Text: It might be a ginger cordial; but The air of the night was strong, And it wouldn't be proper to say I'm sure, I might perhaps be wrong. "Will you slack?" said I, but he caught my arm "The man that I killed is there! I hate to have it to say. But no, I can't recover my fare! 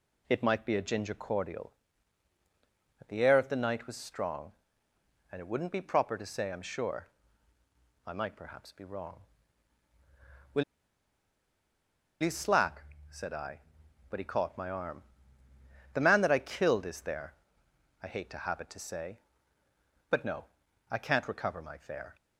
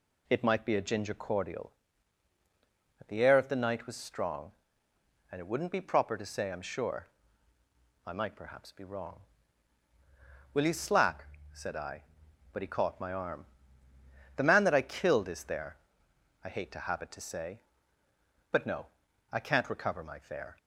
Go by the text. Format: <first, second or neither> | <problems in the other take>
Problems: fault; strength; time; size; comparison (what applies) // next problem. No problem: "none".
second | pauses between "Will" and "you"; strong; at 10.6 s; 1.5 s long // pauses between "arm" and "The"; noticeable; at 15.0 s; 0.90 s long; noticeable in the second